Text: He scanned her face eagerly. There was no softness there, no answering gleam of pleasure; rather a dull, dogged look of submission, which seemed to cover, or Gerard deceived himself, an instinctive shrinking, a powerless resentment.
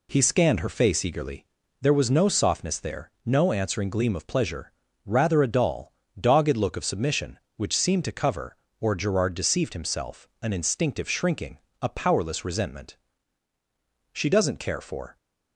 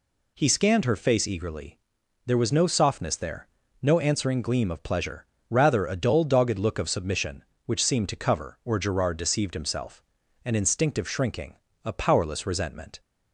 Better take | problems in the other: second | goes on to say "She doesn't care for"; noticeable; from 14.1 s on; 1.0 s long

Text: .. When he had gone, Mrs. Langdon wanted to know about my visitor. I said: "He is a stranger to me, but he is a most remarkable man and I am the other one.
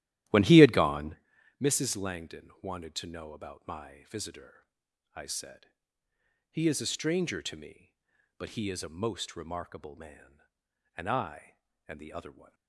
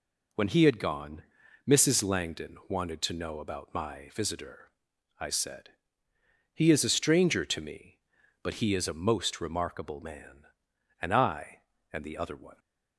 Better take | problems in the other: second | starts louder than the rest; strong; until 1.2 s; 13.5 dB // pauses between "I" and "am"; slight; at 11.5 s; 0.30 s long; slight in the second

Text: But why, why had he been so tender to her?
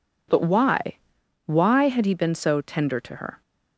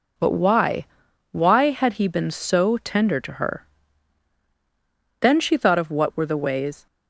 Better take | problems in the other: first | goes on to say "Then she thought of what were the ways"; from 5.2 s on; 1.6 s long

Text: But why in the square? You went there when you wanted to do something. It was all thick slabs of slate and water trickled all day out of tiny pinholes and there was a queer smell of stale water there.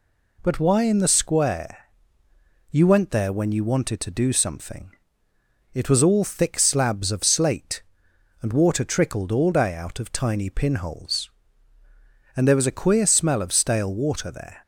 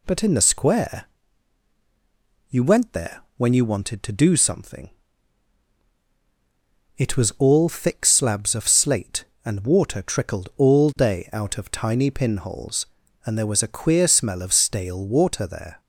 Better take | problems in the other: first | skips "why"; at 0.2 s // pauses between "there" and "when"; slight; at 3.2 s; 0.16 s long

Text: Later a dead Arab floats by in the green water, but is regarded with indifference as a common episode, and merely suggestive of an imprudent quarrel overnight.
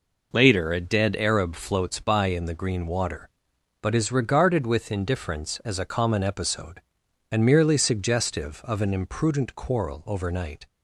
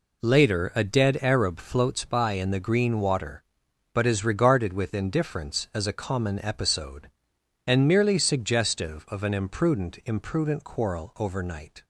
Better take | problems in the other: first | says "imprudent" twice; at 10.0 s

